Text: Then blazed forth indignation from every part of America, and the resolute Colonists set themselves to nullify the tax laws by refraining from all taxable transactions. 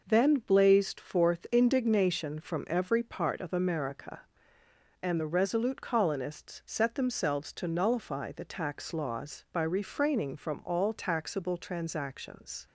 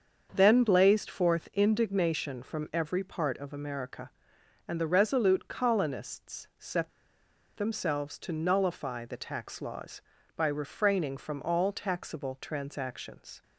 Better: first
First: none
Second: starts louder than the rest; until 1.3 s; 6.5 dB // pauses between "set" and "themselves"; noticeable; at 6.8 s; 0.67 s long

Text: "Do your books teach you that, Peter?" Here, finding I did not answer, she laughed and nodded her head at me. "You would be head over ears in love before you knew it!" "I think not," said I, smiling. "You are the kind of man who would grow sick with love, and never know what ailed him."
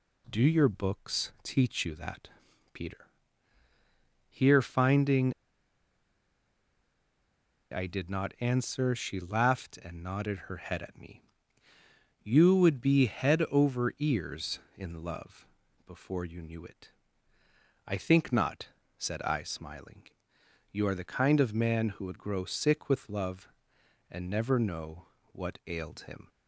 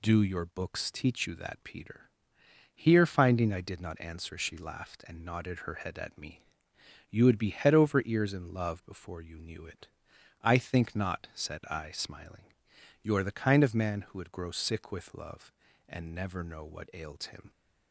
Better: second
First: pauses between "finding" and "I"; strong; at 5.3 s; 2.3 s long // pauses between "love" and "before"; at 15.4 s; 0.42 s long // pauses between "know" and "what"; slight; at 25.0 s; 0.24 s long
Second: none

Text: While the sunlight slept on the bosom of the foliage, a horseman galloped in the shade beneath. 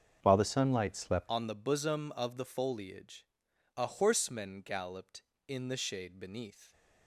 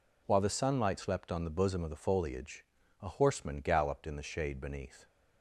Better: second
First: starts louder than the rest; until 1.2 s; 7 dB // changes voice at "on"; from 1.2 s on; 5.5 s long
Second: none

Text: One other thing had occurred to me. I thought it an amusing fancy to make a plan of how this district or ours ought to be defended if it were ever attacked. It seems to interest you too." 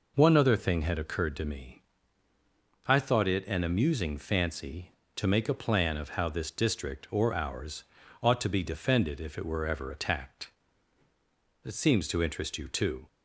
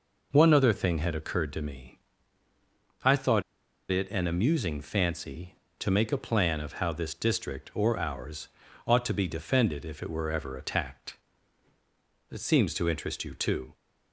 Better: first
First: pauses between "ours" and "ought"; at 7.8 s; 0.40 s long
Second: pauses between "thought" and "it"; noticeable; at 3.4 s; 0.49 s long // pauses between "ours" and "ought"; at 8.4 s; 0.40 s long

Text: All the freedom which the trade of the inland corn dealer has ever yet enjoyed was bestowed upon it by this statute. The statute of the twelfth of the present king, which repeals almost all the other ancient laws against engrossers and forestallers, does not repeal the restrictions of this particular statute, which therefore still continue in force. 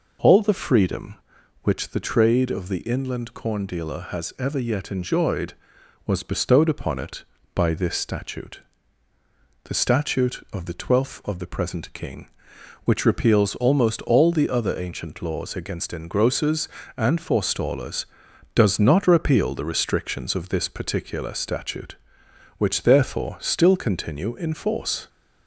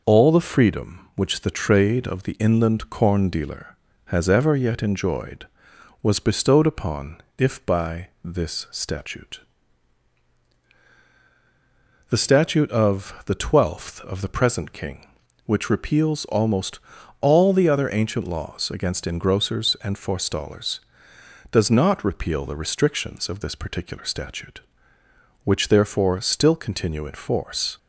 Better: first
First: none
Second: says "if" for "it"; at 7.3 s // pauses between "almost" and "all"; at 16.7 s; 0.42 s long

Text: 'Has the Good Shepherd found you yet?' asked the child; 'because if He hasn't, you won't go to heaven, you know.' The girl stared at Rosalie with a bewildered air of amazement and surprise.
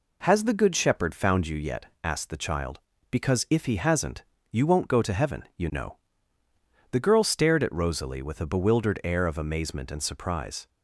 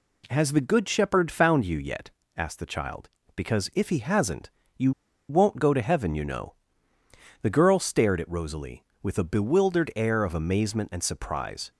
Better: first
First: none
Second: pauses between "you" and "won't"; at 4.9 s; 0.38 s long

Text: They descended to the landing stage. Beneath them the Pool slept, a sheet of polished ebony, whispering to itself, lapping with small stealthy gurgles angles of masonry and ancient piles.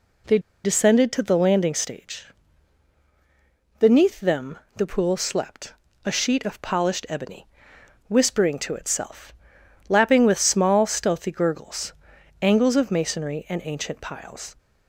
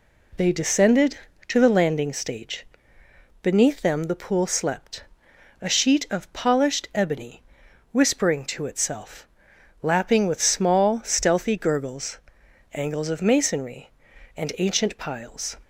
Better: second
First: pauses between "They" and "descended"; slight; at 0.3 s; 0.25 s long // pauses between "them" and "the"; slight; at 4.5 s; 0.18 s long // pauses between "gurgles" and "angles"; noticeable; at 11.9 s; 0.48 s long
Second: pauses between "gurgles" and "angles"; noticeable; at 12.1 s; 0.54 s long

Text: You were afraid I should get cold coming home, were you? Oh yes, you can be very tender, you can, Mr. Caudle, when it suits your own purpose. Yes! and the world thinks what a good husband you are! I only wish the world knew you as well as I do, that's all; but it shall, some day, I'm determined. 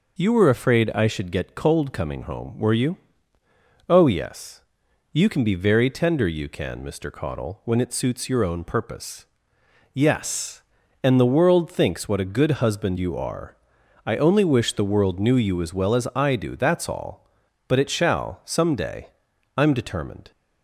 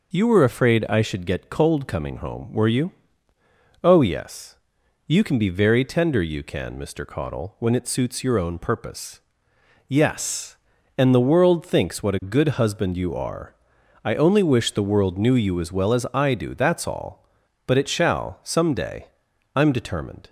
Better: neither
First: none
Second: none

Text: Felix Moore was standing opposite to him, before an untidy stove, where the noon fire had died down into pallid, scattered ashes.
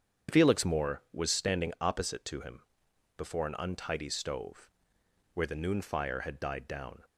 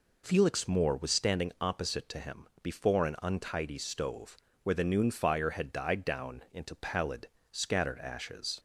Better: second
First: starts louder than the rest; strong; until 1.4 s; 7.5 dB // stops before "into pallid scattered ashes"; at 7.0 s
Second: none

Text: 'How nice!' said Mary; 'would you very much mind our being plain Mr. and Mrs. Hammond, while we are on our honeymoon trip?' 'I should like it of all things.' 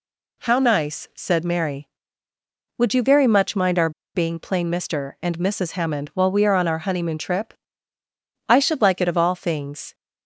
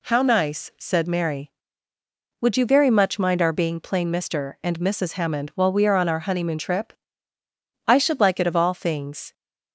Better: second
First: pauses between "our" and "being"; slight; at 3.8 s; 0.25 s long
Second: none

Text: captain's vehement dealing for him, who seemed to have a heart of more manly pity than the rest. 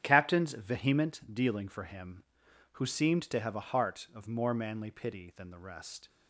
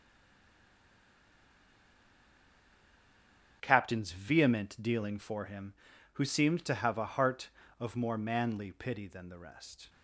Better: first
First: starts louder than the rest; strong; until 1.0 s; 9.5 dB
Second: stays silent before the first word; strong; until 3.6 s; 3.6 s long // starts louder than the rest; strong; until 4.6 s; 8 dB

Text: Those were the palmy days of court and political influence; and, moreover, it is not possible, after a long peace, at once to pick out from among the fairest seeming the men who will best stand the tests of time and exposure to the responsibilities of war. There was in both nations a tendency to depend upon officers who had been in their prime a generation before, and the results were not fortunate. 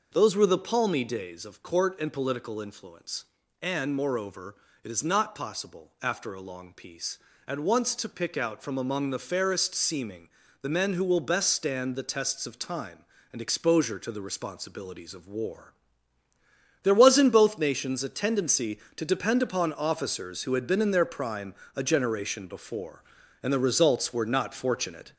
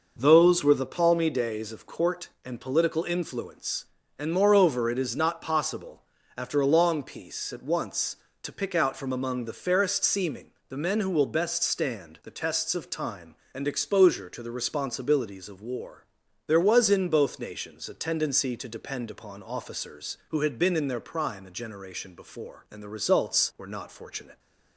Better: second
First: gets louder; throughout; 3.5 dB // pauses between "seeming" and "the"; slight; at 10.2 s; 0.34 s long // pauses between "prime" and "a"; slight; at 21.5 s; 0.20 s long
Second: pauses between "seeming" and "the"; slight; at 10.4 s; 0.22 s long

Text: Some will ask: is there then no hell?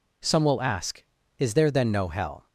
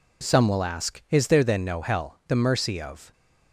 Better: first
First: none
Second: goes on to say "The mercy of"; noticeable; from 2.2 s on; 0.84 s long

